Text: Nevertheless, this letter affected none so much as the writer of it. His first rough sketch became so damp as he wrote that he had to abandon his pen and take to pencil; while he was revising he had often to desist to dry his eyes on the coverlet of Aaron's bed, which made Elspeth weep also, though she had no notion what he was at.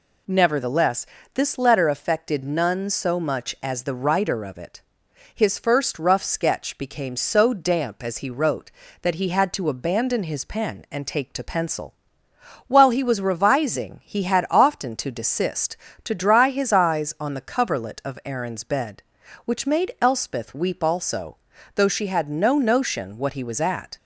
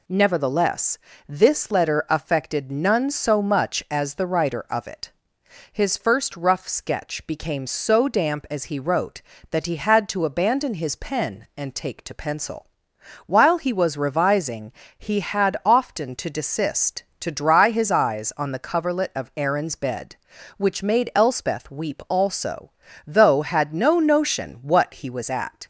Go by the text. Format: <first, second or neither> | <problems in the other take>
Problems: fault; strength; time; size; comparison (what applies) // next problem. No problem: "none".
first | pauses between "revising" and "he"; slight; at 14.7 s; 0.24 s long // skips "she"; at 23.4 s